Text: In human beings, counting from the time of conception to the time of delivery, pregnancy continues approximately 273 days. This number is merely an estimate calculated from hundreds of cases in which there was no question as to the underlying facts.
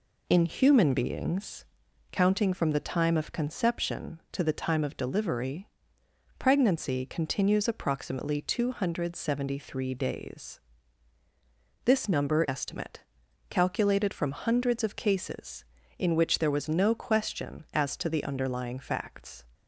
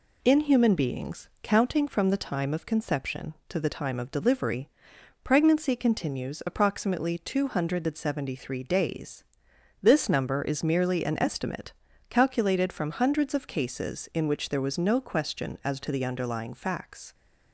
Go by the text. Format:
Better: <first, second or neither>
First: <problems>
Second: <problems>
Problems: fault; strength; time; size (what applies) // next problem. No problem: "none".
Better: second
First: skips "is merely an"; at 12.4 s // pauses between "estimate" and "calculated"; noticeable; at 13.0 s; 0.48 s long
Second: pauses between "estimate" and "calculated"; at 11.7 s; 0.38 s long